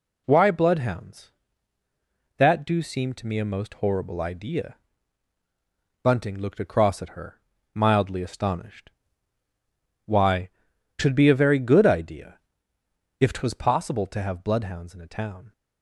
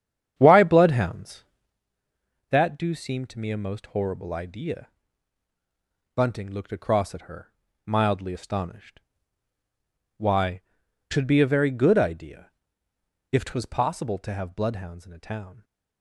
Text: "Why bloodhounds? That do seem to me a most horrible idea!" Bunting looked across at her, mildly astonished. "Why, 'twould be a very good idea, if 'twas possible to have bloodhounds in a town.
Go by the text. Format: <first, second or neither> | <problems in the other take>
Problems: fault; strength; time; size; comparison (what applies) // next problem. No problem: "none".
first | starts louder than the rest; strong; until 1.8 s; 9 dB